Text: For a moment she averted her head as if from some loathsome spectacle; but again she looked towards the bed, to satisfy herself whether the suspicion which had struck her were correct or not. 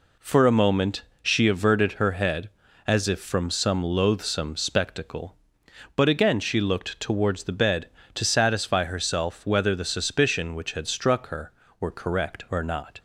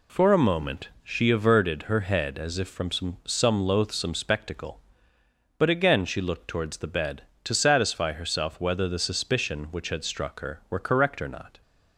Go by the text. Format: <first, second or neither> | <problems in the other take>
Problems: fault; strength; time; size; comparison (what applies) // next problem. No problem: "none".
first | pauses between "moment" and "she"; slight; at 0.8 s; 0.16 s long; slight in the first // says "some" twice; at 3.2 s